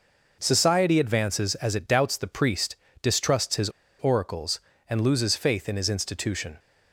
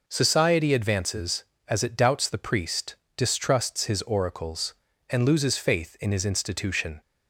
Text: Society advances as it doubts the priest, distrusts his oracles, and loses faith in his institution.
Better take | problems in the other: second | pauses between "his" and "oracles"; slight; at 3.6 s; 0.31 s long

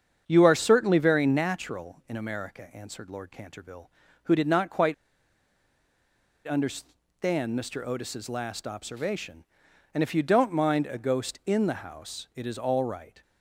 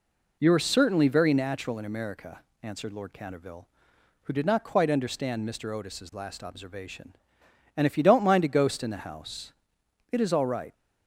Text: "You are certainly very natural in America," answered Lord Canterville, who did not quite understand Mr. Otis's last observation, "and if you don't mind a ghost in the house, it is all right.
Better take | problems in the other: second | starts louder than the rest; strong; until 1.2 s; 7.5 dB // pauses between "quite" and "understand"; strong; at 4.9 s; 1.5 s long

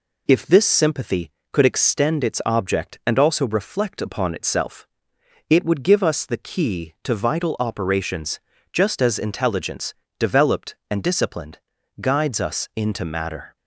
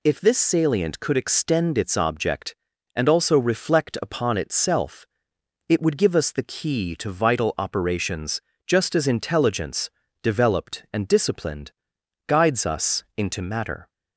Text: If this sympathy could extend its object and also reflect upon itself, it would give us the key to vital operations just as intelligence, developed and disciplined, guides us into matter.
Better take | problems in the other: first | says "salient" for "sympathy"; at 0.3 s // pauses between "operations" and "just"; slight; at 8.4 s; 0.24 s long; slight in the first

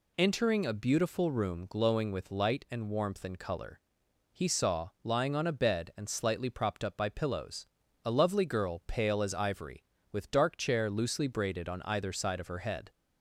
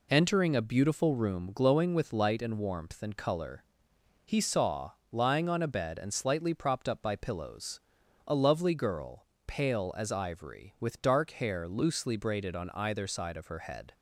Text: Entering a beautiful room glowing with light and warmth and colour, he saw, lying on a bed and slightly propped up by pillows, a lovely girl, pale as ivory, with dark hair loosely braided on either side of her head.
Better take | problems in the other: second | says "chair" for "hair"; at 10.5 s

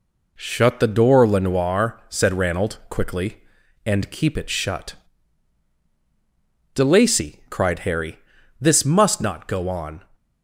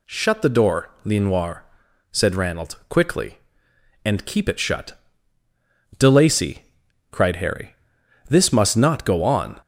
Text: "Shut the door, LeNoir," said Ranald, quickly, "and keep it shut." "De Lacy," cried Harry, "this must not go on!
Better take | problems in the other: neither | none

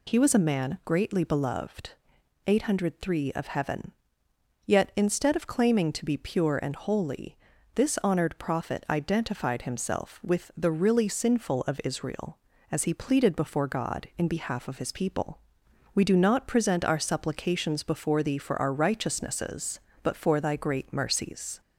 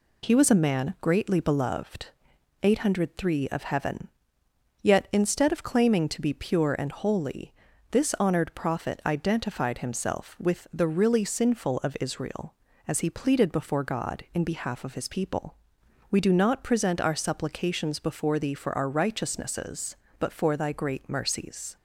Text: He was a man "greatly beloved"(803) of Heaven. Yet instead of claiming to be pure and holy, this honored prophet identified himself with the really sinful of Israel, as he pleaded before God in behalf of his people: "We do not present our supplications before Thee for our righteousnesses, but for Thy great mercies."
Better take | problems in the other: second | gets louder; noticeable; throughout; 4 dB

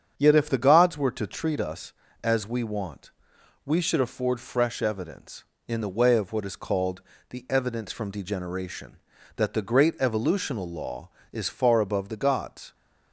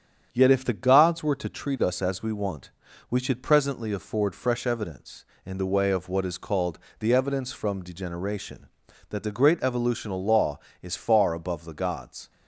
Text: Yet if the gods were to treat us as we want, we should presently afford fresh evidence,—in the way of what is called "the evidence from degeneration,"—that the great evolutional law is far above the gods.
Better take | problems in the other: second | starts louder than the rest; strong; until 1.1 s; 8 dB; strong in the second // skips "presently"; at 3.9 s // pauses between "called" and "the"; slight; at 7.0 s; 0.28 s long; slight in the second

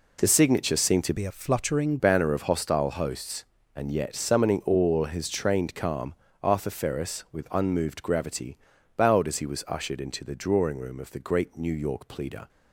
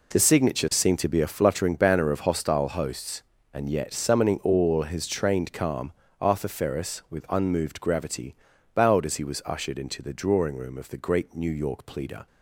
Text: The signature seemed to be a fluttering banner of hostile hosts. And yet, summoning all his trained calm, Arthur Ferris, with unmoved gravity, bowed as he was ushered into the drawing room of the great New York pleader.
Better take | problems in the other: second | changes voice from "be" to "fluttering"; from 1.1 to 1.9 s; 0.8 s long

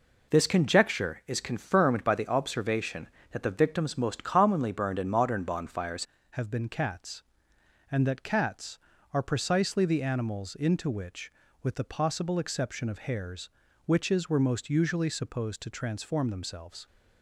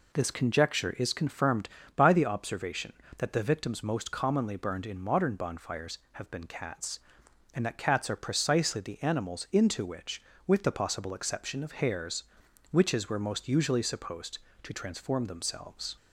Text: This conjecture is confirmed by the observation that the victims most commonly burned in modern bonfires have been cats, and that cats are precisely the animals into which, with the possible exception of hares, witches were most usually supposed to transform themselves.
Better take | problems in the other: second | changes voice at "have"; from 6.3 s on; 10.5 s long

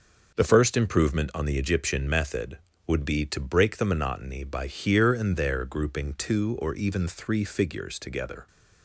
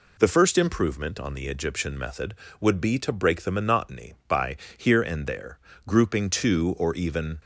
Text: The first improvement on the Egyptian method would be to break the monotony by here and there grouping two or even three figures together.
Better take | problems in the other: first | pauses between "by" and "here"; slight; at 4.5 s; 0.18 s long // pauses between "there" and "grouping"; slight; at 5.5 s; 0.30 s long // stops before "three figures together"; at 7.4 s

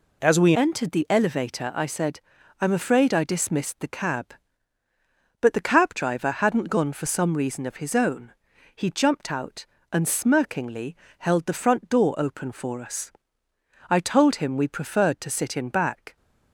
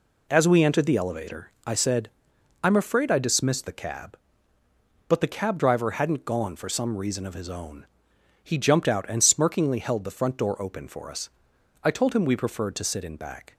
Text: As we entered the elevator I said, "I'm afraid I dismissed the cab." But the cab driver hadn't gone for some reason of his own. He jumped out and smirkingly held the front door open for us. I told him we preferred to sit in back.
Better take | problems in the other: second | changes voice at "entered"; from 0.5 s on; 15.6 s long // pauses between "smirkingly" and "held"; slight; at 10.9 s; 0.24 s long

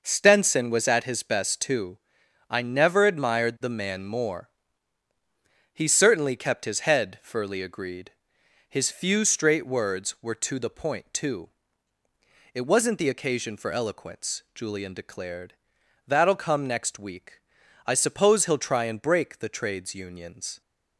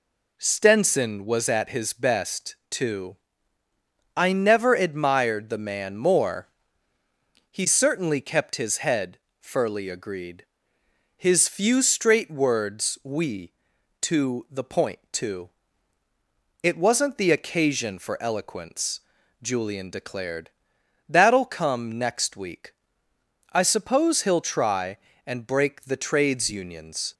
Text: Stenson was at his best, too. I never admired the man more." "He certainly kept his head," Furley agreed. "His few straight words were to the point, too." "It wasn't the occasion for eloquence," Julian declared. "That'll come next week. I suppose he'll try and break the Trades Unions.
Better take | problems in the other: first | says "we" for "were"; at 13.0 s

